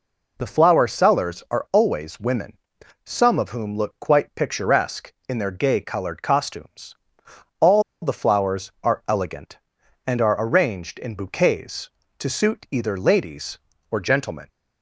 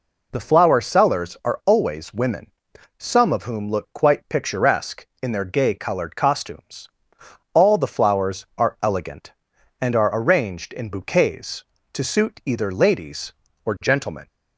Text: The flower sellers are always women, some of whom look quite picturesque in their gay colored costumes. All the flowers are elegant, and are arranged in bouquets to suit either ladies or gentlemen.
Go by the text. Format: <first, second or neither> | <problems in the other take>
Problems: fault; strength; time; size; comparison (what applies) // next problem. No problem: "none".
second | pauses between "All" and "the"; slight; at 7.8 s; 0.21 s long